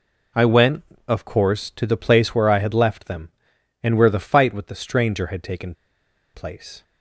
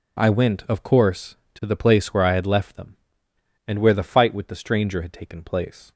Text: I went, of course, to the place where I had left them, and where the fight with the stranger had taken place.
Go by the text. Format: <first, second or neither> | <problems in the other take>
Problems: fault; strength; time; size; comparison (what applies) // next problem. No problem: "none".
second | pauses between "taken" and "place"; noticeable; at 5.7 s; 0.61 s long